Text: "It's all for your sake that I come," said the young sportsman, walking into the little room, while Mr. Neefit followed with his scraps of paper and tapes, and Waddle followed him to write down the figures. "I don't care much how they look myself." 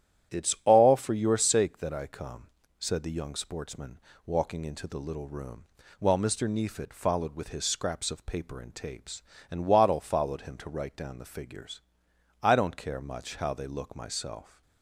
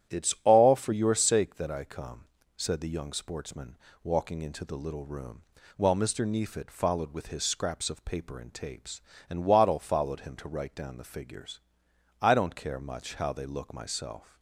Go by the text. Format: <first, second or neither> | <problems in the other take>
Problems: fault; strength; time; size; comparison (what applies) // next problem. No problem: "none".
neither | starts louder than the rest; strong; the same in both